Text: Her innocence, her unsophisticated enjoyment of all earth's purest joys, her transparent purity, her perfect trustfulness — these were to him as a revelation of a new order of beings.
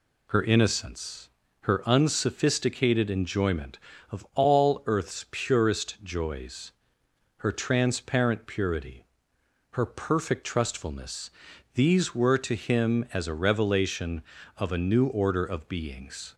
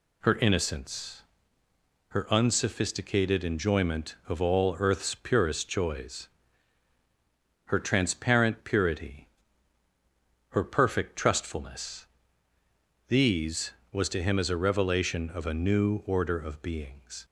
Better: first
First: none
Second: says "was" for "were"; at 13.9 s

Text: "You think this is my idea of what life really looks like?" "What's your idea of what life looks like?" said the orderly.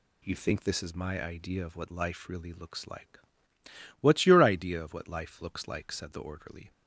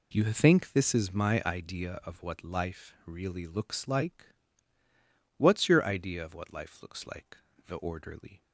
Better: first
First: none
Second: skips "said"; at 7.5 s

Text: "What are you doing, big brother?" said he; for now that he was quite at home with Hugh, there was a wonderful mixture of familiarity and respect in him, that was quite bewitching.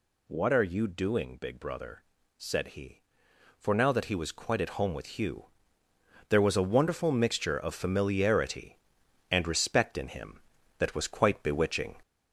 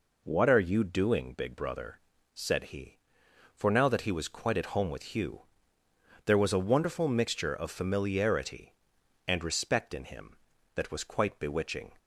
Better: second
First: gets louder; slight; throughout; 3 dB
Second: none

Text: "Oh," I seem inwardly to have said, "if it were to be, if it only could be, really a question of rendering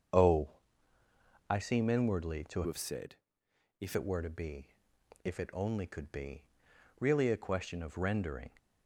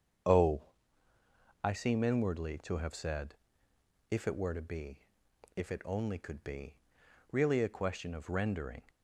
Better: second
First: starts louder than the rest; strong; until 2.1 s; 7 dB // changes voice from "have" to "if"; from 2.6 to 3.9 s; 1.3 s long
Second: starts louder than the rest; strong; until 2.2 s; 7 dB

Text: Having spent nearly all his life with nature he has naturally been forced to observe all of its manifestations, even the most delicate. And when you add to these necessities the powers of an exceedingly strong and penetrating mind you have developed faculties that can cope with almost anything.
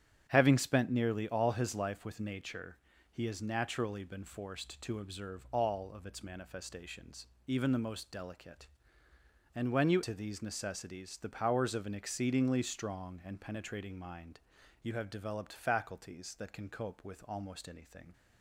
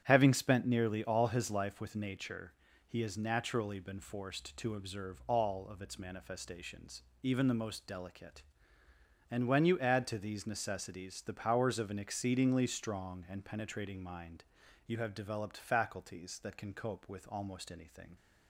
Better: second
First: starts louder than the rest; strong; until 1.2 s; 10 dB // pauses between "nature" and "he"; slight; at 2.7 s; 0.34 s long // skips "add"; at 10.0 s // pauses between "mind" and "you"; at 14.3 s; 0.44 s long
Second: starts louder than the rest; strong; until 1.0 s; 9.5 dB // pauses between "nature" and "he"; slight; at 2.5 s; 0.34 s long // pauses between "mind" and "you"; at 14.4 s; 0.44 s long

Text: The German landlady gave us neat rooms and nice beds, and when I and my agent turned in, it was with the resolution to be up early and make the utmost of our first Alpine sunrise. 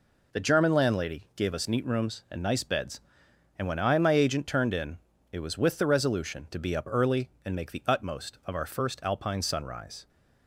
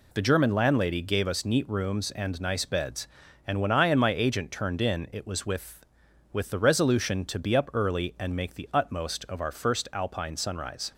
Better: first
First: none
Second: says "with" twice; at 6.3 s

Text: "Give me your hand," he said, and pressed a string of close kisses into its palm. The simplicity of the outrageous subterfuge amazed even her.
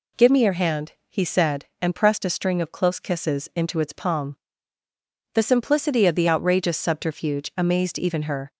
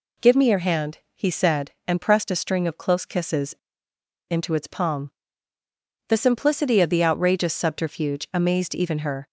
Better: first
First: none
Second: pauses between "kisses" and "into"; noticeable; at 3.5 s; 0.76 s long

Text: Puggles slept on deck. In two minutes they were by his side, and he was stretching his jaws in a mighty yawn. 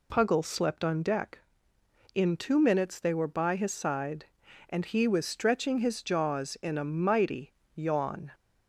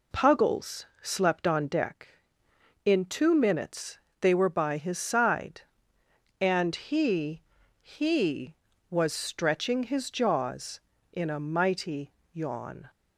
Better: first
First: pauses between "mighty" and "yawn"; slight; at 7.5 s; 0.22 s long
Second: pauses between "Puggles" and "slept"; slight; at 0.8 s; 0.18 s long // pauses between "minutes" and "they"; slight; at 3.9 s; 0.22 s long // says "he" twice; at 7.7 s // pauses between "mighty" and "yawn"; slight; at 12.1 s; 0.20 s long

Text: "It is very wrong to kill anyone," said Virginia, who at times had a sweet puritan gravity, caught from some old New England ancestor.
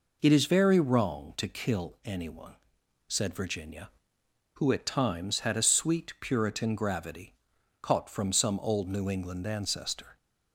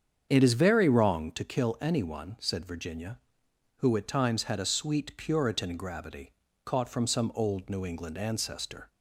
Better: first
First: none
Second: starts louder than the rest; strong; until 1.5 s; 7.5 dB

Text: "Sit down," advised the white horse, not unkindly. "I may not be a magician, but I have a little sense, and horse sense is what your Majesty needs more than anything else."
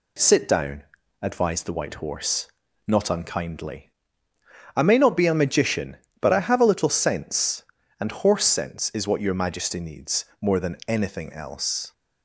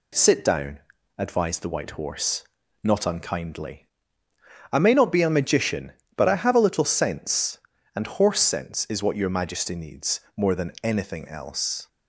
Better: neither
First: pauses between "needs" and "more"; slight; at 10.2 s; 0.16 s long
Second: pauses between "needs" and "more"; slight; at 10.1 s; 0.16 s long

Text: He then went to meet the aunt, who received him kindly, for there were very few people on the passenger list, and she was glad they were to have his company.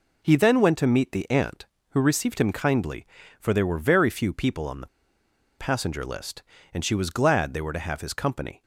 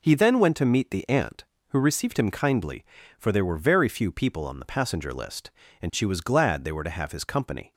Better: second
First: pauses between "the" and "passenger"; noticeable; at 4.8 s; 0.73 s long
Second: none

